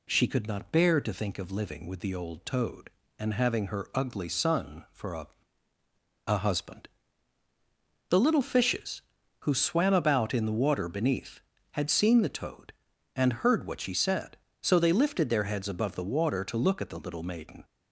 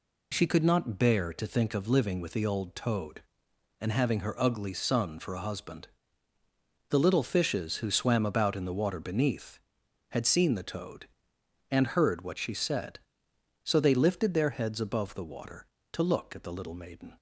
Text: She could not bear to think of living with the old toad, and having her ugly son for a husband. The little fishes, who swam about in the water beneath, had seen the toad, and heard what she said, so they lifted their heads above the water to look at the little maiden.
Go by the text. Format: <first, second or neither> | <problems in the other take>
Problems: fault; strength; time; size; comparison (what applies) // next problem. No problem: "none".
second | says "a" twice; at 6.2 s